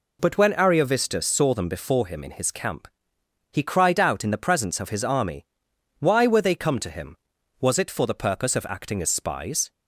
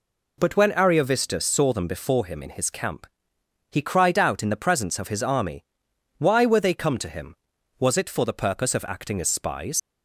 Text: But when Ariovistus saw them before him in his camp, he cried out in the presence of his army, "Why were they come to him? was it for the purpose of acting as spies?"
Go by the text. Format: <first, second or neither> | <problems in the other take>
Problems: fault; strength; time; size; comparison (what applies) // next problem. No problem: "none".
first | leaves "spies" unfinished; at 9.7 s; 95 ms